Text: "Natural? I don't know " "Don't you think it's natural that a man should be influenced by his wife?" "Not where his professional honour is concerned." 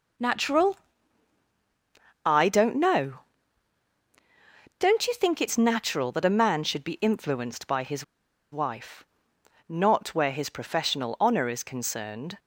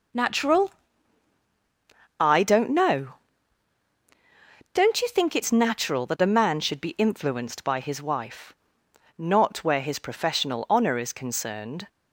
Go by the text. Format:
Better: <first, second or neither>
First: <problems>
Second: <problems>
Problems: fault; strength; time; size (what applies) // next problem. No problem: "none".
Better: second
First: pauses between "his" and "wife"; noticeable; at 8.0 s; 0.49 s long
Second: none